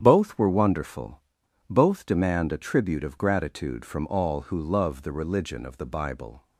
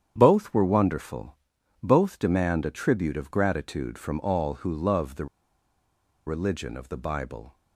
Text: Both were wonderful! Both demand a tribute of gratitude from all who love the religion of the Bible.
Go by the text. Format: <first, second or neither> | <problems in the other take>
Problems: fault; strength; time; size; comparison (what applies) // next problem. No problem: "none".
first | starts louder than the rest; strong; until 1.1 s; 9 dB; strong in the first // pauses between "the" and "religion"; at 5.2 s; 0.99 s long